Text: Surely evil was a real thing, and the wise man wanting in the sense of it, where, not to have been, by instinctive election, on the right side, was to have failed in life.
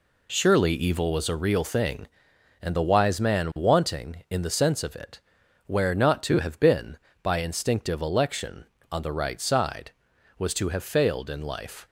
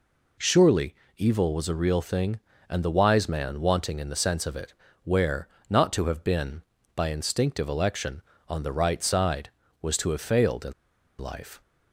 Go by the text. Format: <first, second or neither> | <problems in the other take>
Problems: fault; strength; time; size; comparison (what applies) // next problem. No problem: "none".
first | pauses between "Surely" and "evil"; slight; at 0.9 s; 0.22 s long // pauses between "in" and "life"; noticeable; at 10.7 s; 0.46 s long